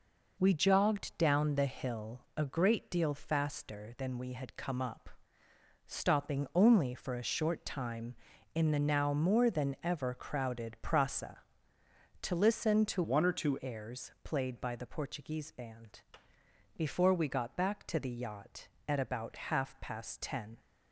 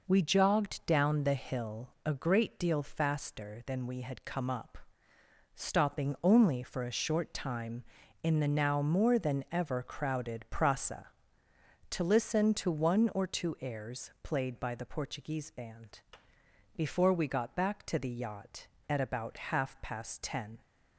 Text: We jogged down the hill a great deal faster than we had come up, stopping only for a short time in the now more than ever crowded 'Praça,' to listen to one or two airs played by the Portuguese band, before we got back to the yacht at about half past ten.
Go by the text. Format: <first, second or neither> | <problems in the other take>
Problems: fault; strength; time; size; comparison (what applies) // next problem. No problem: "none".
second | pauses between "hill" and "a"; slight; at 2.2 s; 0.16 s long; slight in the second // changes voice from "one" to "two"; from 13.0 to 13.5 s; 0.5 s long